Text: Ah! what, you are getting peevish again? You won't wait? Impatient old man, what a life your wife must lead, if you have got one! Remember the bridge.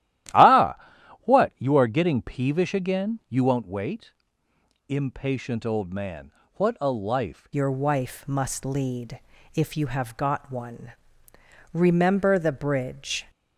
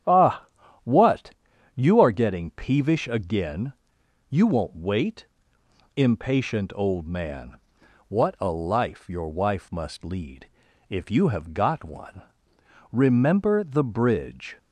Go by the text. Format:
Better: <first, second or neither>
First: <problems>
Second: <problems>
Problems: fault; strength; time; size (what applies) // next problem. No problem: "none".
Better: second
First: starts louder than the rest; strong; until 1.8 s; 13.5 dB // changes voice at "your"; from 7.5 s on; 5.7 s long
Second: starts louder than the rest; strong; until 1.8 s; 9.5 dB